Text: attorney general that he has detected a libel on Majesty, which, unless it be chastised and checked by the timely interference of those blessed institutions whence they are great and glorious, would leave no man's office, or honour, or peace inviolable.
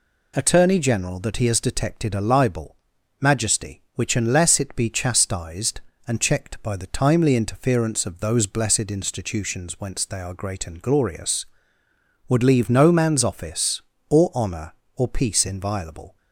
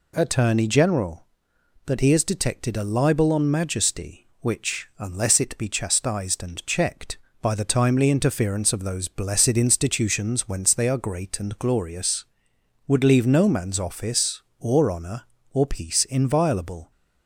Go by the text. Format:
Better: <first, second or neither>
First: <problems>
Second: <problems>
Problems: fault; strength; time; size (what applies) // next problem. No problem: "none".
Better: second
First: skips "on"; at 2.9 s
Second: none